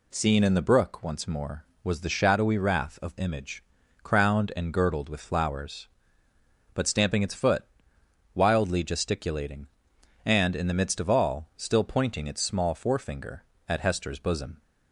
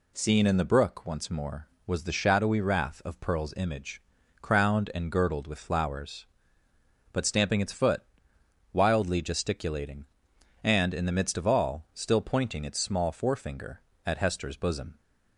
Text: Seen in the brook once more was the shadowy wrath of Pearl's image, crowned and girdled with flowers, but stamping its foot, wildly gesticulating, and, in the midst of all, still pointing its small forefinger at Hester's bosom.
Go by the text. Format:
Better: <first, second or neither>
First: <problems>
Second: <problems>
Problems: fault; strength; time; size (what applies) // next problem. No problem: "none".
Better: second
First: skips "Pearl's"; at 3.1 s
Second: none